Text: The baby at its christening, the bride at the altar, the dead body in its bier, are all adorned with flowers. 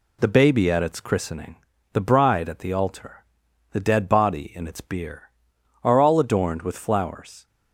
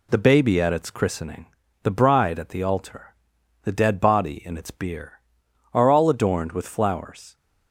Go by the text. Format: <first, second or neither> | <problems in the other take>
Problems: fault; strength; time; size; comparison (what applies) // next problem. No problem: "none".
neither | none